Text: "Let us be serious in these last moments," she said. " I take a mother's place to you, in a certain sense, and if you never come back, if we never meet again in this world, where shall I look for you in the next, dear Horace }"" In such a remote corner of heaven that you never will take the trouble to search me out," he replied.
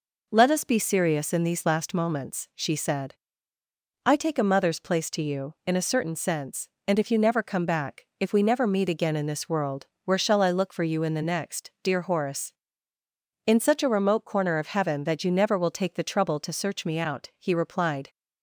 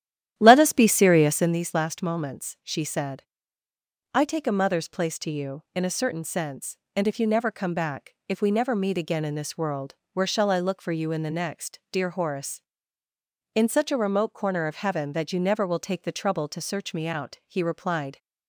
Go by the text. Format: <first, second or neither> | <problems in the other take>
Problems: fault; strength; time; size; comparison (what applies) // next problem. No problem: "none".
first | starts louder than the rest; strong; until 1.6 s; 11 dB